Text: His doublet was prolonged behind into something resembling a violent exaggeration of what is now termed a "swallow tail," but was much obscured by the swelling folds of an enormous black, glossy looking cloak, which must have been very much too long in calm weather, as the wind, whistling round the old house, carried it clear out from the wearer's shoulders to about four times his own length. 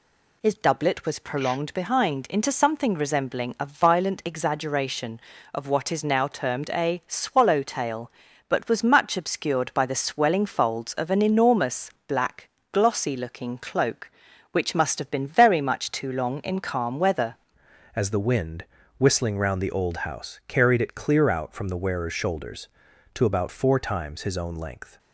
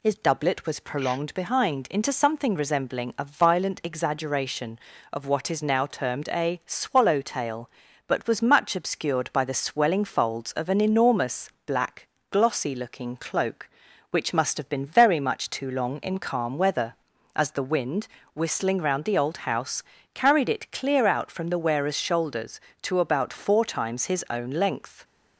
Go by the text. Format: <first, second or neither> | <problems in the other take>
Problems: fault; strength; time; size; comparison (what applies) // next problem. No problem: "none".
second | pauses between "enormous" and "black"; slight; at 11.8 s; 0.16 s long; slight in the second // changes voice at "as"; from 17.9 s on; 7.0 s long